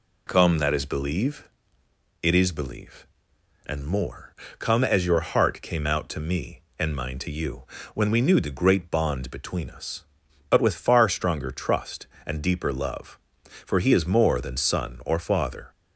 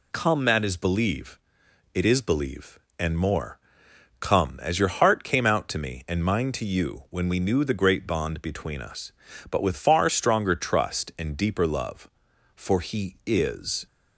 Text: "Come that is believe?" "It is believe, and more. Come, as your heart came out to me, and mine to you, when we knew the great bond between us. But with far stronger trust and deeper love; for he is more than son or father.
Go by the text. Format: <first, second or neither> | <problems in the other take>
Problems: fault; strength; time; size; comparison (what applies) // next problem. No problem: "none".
first | stops before "more than son or father"; at 13.8 s